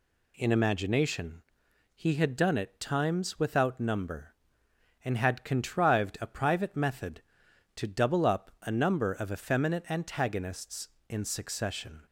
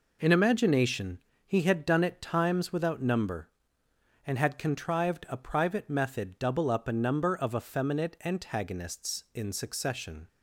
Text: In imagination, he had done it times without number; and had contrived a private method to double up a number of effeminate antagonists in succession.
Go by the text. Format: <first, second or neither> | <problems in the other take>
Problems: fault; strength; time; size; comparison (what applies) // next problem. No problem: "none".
first | skips "to"; at 6.3 s